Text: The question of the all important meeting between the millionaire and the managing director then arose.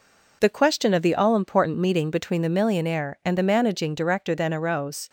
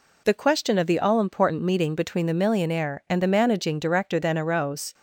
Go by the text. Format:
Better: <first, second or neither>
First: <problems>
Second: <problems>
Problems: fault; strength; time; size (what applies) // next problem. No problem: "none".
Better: second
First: gets quieter; throughout; 4 dB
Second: none